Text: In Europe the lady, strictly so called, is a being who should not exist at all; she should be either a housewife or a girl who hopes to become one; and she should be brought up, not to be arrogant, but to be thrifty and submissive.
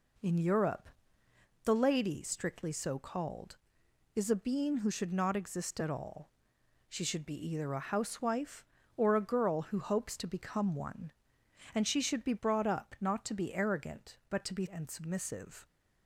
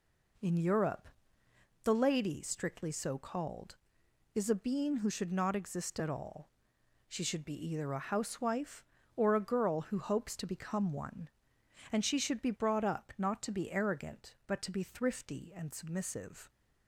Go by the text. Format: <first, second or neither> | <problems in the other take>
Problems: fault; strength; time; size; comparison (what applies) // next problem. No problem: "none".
second | pauses between "Europe" and "the"; noticeable; at 0.8 s; 0.76 s long; noticeable in the second // skips "thrifty"; at 14.6 s